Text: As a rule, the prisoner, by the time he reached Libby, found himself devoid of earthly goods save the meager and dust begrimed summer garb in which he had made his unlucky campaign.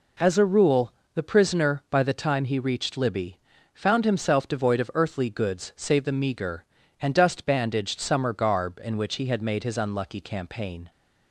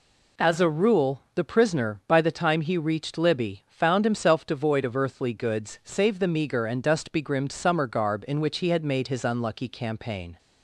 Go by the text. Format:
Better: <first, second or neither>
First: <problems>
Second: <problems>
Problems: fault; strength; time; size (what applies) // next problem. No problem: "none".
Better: second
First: says "bandaged" for "begrimed"; at 7.4 s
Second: none